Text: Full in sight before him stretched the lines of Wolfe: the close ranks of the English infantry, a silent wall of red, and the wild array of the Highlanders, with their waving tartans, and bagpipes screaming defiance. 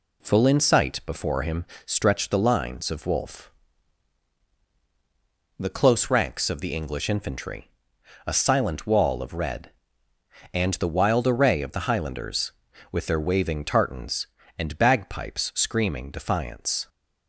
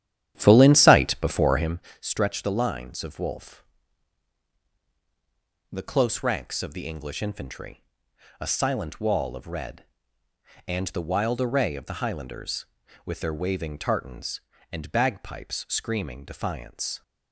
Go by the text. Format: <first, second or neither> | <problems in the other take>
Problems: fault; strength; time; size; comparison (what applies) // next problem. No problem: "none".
first | starts louder than the rest; strong; until 1.8 s; 11 dB // pauses between "him" and "stretched"; slight; at 1.7 s; 0.20 s long; slight in the first